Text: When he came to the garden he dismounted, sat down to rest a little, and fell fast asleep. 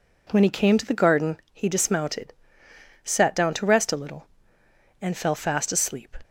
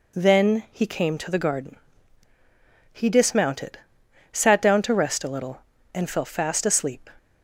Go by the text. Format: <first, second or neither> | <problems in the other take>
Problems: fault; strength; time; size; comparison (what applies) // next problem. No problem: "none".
first | says "Then" for "When"; at 0.1 s // pauses between "garden" and "he"; at 1.7 s; 1.2 s long